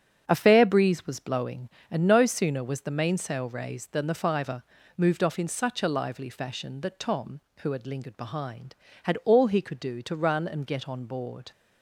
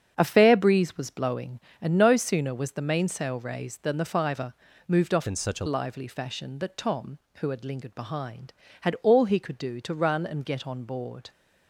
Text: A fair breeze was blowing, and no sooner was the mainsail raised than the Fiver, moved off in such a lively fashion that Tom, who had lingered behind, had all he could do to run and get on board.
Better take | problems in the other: first | starts louder than the rest; strong; until 1.1 s; 7.5 dB; strong in the first // changes voice from "in" to "a"; from 5.2 to 5.6 s; 0.4 s long

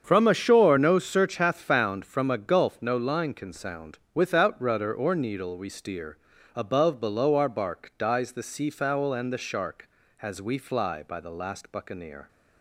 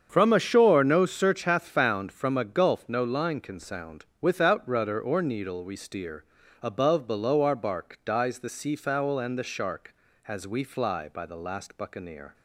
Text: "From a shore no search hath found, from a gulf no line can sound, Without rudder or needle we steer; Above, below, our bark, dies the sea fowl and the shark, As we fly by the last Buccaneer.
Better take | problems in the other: neither | starts louder than the rest; strong; the same in both

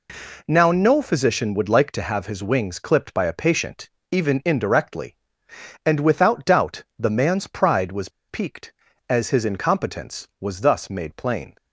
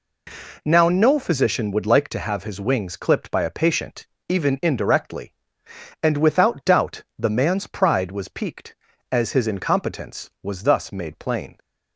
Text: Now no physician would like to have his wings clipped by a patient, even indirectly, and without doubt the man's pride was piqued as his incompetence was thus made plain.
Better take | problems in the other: second | pauses between "doubt" and "the"; slight; at 6.8 s; 0.16 s long; slight in the second // pauses between "was" and "piqued"; slight; at 8.0 s; 0.19 s long

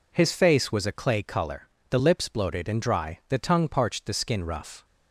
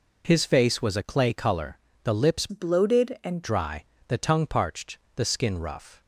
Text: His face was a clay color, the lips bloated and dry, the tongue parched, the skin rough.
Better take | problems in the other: first | changes voice from "bloated" to "and"; from 2.4 to 3.4 s; 1.0 s long

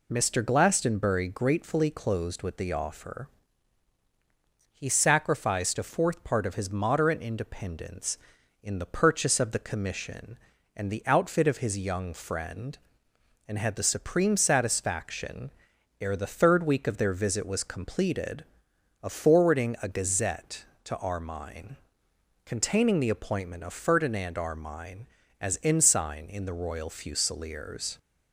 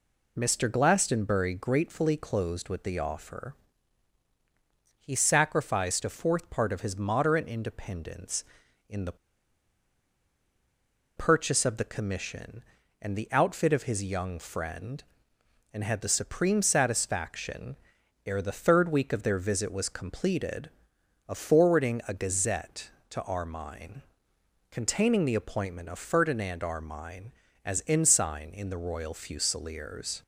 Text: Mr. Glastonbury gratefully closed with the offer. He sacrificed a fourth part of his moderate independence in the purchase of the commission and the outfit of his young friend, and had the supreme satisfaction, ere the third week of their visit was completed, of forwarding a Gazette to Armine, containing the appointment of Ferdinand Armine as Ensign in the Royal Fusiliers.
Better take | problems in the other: first | pauses between "the" and "purchase"; strong; at 9.1 s; 2.0 s long

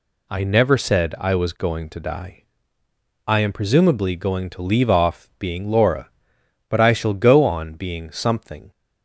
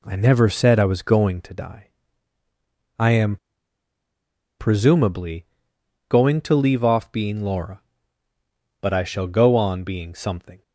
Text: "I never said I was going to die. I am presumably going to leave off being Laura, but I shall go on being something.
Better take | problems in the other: first | pauses between "am" and "presumably"; at 3.3 s; 1.2 s long // pauses between "presumably" and "going"; noticeable; at 5.4 s; 0.62 s long

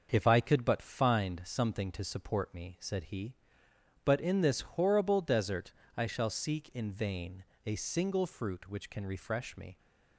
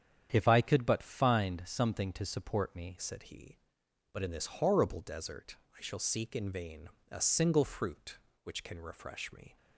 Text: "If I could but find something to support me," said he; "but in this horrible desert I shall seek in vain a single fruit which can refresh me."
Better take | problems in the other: first | starts louder than the rest; strong; until 1.3 s; 8.5 dB; also in the first // changes voice at "said"; from 3.0 s on; 6.5 s long // pauses between "desert" and "I"; slight; at 5.5 s; 0.20 s long; slight in the first // pauses between "vain" and "a"; slight; at 6.8 s; 0.22 s long; slight in the first

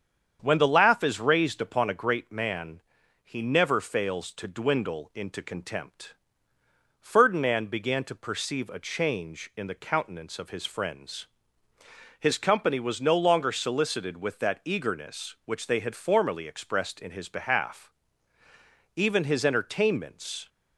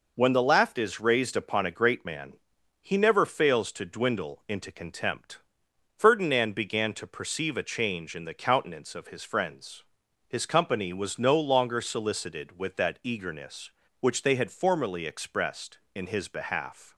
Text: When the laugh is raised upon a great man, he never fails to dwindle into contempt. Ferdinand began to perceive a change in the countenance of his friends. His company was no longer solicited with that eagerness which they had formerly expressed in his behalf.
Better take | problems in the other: second | starts louder than the rest; strong; until 1.4 s; 8 dB // goes on to say "Even his entertainments"; from 18.9 s on; 1.5 s long

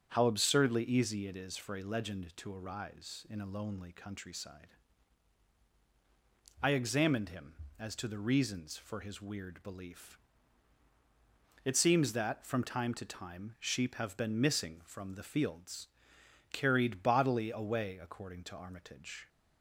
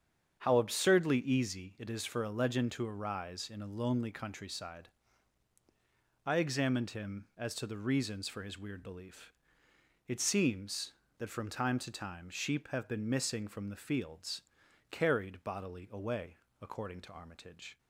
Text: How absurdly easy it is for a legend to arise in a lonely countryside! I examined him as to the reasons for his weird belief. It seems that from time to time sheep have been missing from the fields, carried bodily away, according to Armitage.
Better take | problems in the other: neither | starts louder than the rest; strong; the same in both

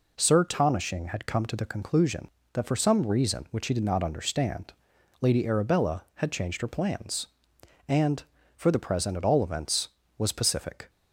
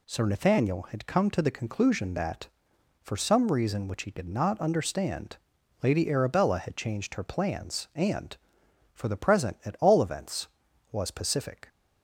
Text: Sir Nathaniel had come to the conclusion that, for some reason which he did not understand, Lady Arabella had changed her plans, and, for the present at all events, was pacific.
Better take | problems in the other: second | says "Tonishing" for "Nathaniel"; at 0.4 s

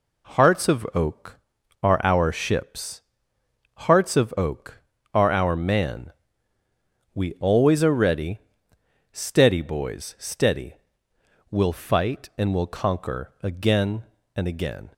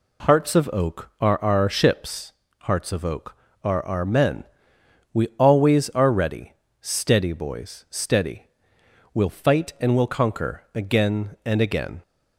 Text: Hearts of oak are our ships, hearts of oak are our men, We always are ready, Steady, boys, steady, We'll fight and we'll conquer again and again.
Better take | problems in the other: second | says "man" for "men"; at 5.5 s

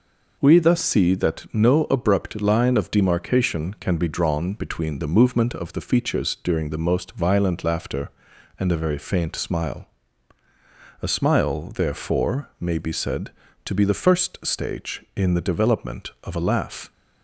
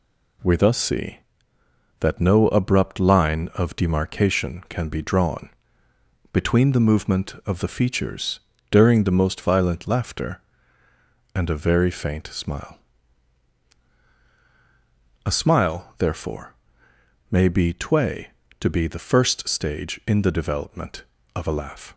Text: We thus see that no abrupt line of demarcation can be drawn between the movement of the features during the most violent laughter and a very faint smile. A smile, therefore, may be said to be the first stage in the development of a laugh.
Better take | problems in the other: first | pauses between "drawn" and "between"; noticeable; at 5.5 s; 0.82 s long // pauses between "features" and "during"; slight; at 8.4 s; 0.30 s long // says "tway" for "said"; at 17.7 s

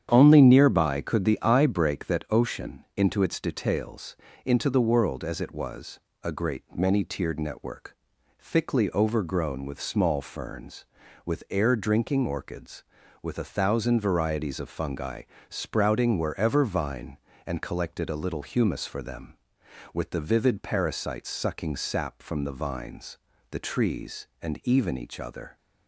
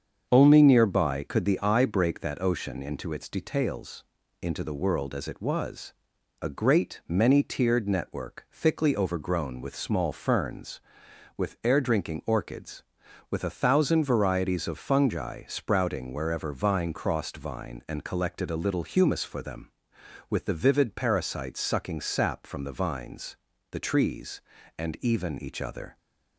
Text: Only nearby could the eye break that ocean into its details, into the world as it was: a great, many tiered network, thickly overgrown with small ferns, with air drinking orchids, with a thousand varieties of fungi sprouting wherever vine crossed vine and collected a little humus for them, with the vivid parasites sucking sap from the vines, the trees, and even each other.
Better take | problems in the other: second | starts louder than the rest; strong; until 1.1 s; 9 dB; strong in the second // pauses between "fungi" and "sprouting"; slight; at 15.2 s; 0.26 s long // skips "vine crossed"; at 16.6 s

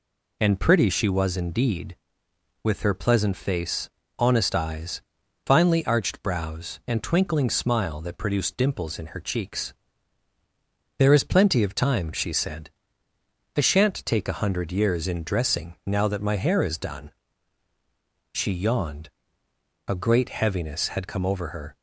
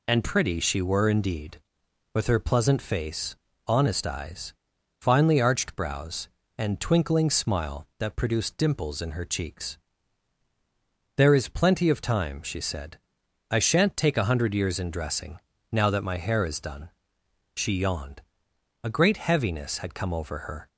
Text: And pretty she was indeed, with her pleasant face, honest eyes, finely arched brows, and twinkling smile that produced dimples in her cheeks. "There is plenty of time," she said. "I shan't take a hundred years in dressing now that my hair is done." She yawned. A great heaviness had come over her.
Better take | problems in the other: first | says "were" for "was"; at 0.8 s // pauses between "dressing" and "now"; slight; at 15.3 s; 0.32 s long

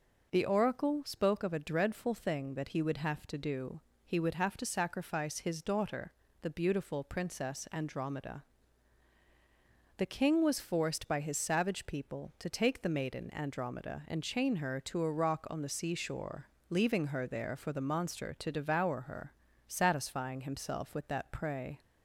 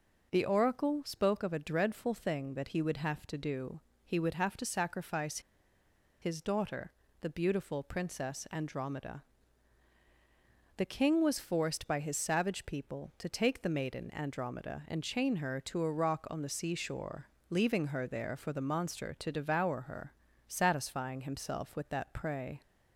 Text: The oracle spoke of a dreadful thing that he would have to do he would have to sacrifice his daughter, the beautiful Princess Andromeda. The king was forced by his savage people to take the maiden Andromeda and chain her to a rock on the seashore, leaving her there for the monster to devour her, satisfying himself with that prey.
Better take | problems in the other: first | pauses between "do" and "he"; slight; at 3.7 s; 0.28 s long; slight in the first // pauses between "sacrifice" and "his"; noticeable; at 5.3 s; 0.82 s long

